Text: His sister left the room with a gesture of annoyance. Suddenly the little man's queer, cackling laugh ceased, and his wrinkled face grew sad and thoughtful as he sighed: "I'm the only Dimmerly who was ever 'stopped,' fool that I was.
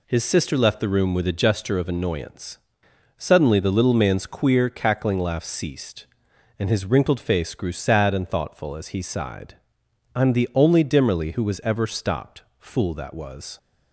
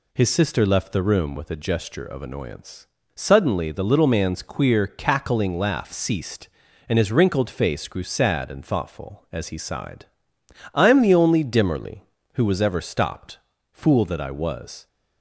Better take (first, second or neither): second